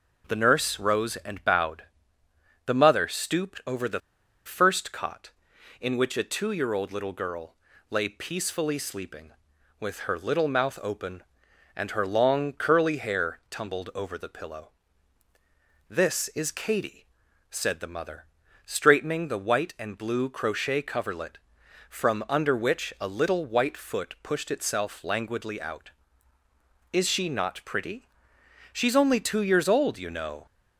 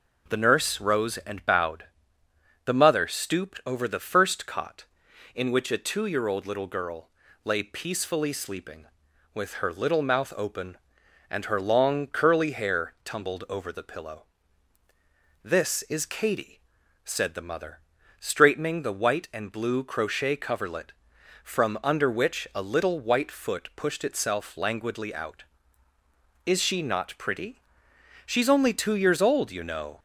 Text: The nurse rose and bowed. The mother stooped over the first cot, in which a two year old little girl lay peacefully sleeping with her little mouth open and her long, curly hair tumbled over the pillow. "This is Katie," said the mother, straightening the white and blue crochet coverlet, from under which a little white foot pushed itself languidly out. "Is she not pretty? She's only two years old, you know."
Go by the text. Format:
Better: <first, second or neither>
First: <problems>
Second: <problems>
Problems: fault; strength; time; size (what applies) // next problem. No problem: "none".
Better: second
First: pauses between "the" and "first"; at 4.0 s; 0.45 s long // pauses between "girl" and "lay"; slight; at 7.5 s; 0.34 s long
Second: pauses between "girl" and "lay"; slight; at 7.0 s; 0.34 s long